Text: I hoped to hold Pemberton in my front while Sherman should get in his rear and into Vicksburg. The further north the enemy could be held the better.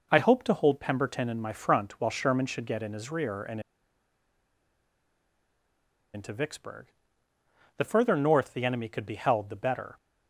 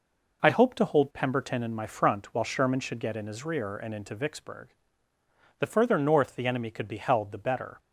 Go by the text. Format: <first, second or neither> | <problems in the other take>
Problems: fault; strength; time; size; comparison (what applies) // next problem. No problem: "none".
second | pauses between "and" and "into"; strong; at 3.6 s; 2.5 s long